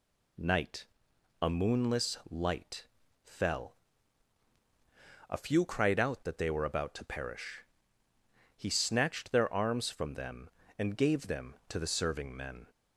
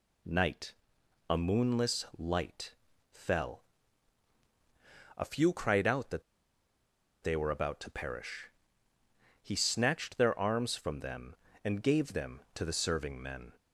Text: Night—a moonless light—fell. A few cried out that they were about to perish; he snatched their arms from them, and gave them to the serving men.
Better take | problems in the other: first | pauses between "that" and "they"; at 6.2 s; 1.0 s long

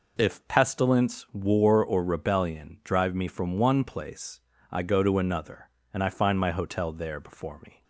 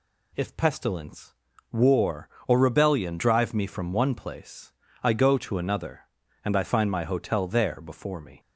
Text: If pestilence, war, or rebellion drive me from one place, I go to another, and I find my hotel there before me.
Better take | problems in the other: neither | none

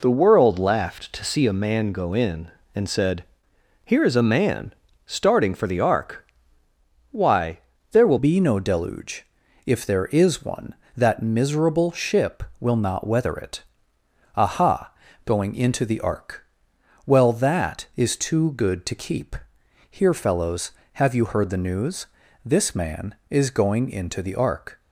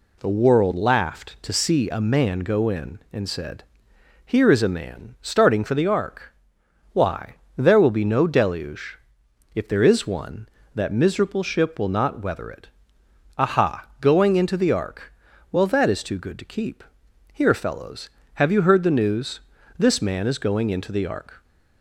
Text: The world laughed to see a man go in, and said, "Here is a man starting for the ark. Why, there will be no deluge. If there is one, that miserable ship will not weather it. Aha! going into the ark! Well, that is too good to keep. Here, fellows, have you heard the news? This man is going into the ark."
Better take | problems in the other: second | pauses between "man" and "starting"; slight; at 4.7 s; 0.32 s long // changes voice at "be"; from 8.1 s on; 16.6 s long

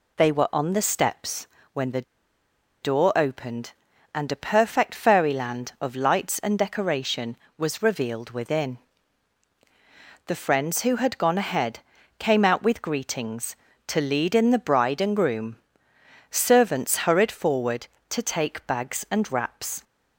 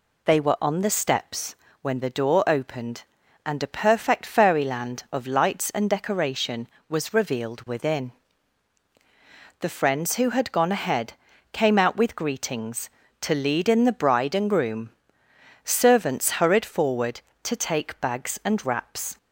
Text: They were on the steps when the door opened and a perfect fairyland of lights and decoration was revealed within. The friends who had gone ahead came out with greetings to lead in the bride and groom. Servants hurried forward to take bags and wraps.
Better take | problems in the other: second | pauses between "steps" and "when"; slight; at 1.4 s; 0.26 s long; slight in the second // pauses between "the" and "door"; noticeable; at 2.0 s; 0.79 s long // pauses between "ahead" and "came"; at 11.7 s; 0.40 s long; also in the second

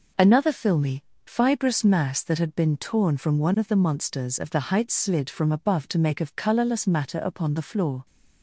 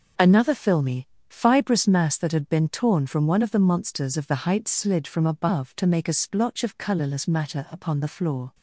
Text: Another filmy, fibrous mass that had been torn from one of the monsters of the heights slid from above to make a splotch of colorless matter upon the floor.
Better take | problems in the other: second | skips "a splotch"; at 6.2 s

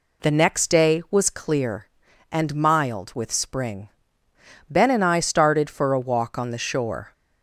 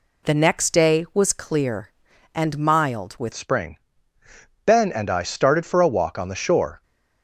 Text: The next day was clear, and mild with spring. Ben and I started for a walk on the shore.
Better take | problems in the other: first | changes voice at "spring"; from 3.3 s on; 3.5 s long

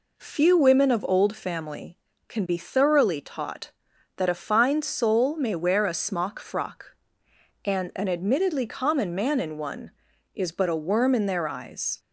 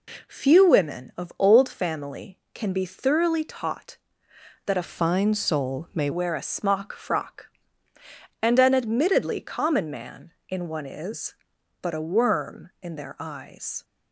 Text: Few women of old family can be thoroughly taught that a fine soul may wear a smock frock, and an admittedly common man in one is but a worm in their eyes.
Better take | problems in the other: first | changes voice from "fine" to "may"; from 4.8 to 6.0 s; 1.2 s long

